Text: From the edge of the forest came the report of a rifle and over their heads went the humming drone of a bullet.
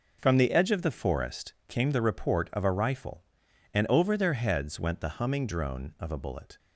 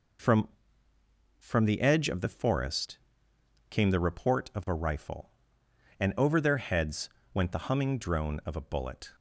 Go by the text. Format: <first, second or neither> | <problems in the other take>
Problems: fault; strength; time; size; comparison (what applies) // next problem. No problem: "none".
first | says "From" twice; at 1.3 s // pauses between "forest" and "came"; noticeable; at 2.9 s; 0.72 s long; slight in the first // pauses between "heads" and "went"; slight; at 7.0 s; 0.24 s long